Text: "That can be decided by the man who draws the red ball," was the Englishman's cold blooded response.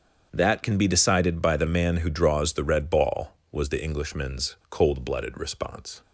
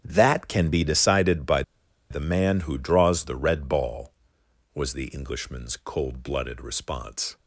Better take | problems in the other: first | starts louder than the rest; strong; until 1.0 s; 9.5 dB; strong in the first // pauses between "by" and "the"; noticeable; at 1.6 s; 0.48 s long

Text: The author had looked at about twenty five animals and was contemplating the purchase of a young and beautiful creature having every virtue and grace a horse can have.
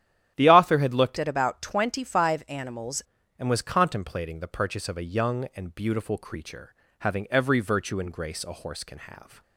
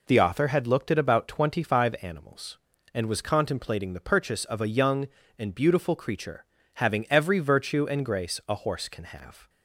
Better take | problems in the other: second | starts louder than the rest; strong; until 1.3 s; 10.5 dB // changes voice from "at" to "animals"; from 1.1 to 3.0 s; 1.9 s long // pauses between "creature" and "having"; slight; at 6.7 s; 0.26 s long; slight in the second

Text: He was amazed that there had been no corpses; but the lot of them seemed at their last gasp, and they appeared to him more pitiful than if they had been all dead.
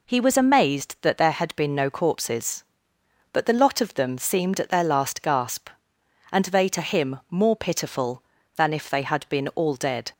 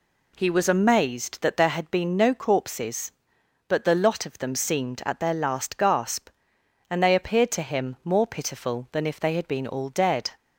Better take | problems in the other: second | skips "appeared"; at 6.6 s

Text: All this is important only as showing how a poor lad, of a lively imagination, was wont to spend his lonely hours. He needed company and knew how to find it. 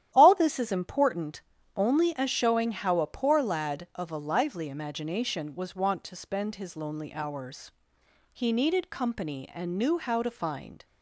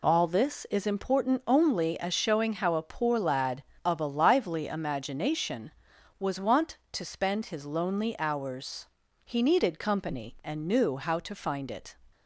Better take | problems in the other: second | starts louder than the rest; strong; until 1.1 s; 11.5 dB // pauses between "important" and "only"; slight; at 1.4 s; 0.34 s long // stops before "it"; at 10.8 s

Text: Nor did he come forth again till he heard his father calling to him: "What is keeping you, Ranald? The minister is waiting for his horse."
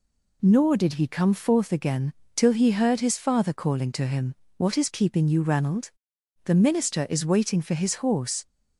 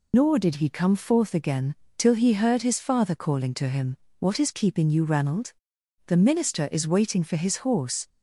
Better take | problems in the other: first | loses the start of "Nor"; at 0.1 s; 100 ms // pauses between "again" and "till"; slight; at 1.7 s; 0.22 s long; slight in the first

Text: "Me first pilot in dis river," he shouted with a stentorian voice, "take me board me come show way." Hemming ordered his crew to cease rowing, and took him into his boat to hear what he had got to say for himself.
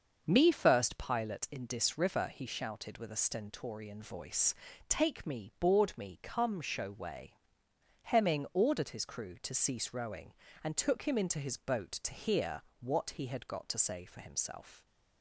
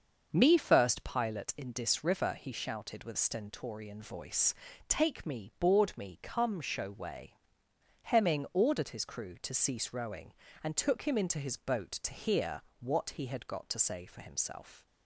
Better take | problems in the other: first | starts louder than the rest; until 1.3 s; 6 dB; also in the first // skips "a"; at 3.1 s // pauses between "hear" and "what"; slight; at 12.6 s; 0.18 s long; slight in the first

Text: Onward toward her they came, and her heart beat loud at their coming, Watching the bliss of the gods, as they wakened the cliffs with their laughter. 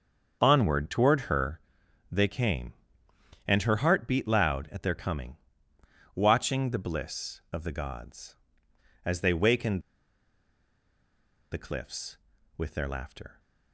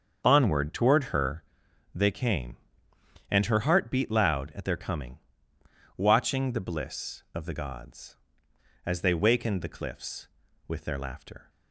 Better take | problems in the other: second | starts louder than the rest; until 1.4 s; 7 dB; also in the second // pauses between "her" and "they"; noticeable; at 1.5 s; 0.50 s long; noticeable in the second // pauses between "wakened" and "the"; strong; at 9.8 s; 1.7 s long

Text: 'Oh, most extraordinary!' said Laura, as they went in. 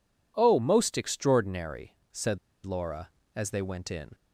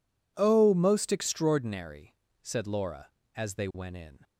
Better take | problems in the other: second | pauses between "said" and "Laura"; slight; at 2.3 s; 0.26 s long

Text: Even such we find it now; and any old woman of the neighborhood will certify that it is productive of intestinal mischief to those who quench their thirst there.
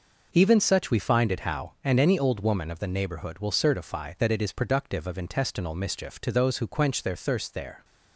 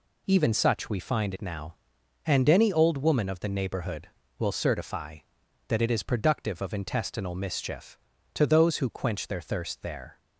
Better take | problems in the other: second | says "how" for "now"; at 1.4 s

